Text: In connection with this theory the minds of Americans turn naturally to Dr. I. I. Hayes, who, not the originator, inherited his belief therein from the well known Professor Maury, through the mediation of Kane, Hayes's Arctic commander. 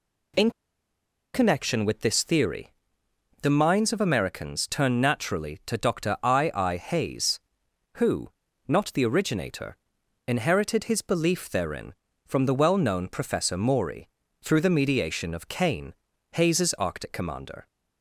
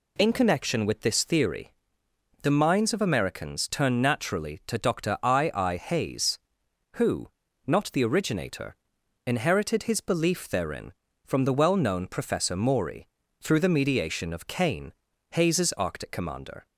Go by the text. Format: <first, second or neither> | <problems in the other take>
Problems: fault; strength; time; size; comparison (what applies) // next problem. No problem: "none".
second | pauses between "In" and "connection"; noticeable; at 0.5 s; 0.83 s long // pauses between "theory" and "the"; noticeable; at 2.7 s; 0.68 s long; noticeable in the second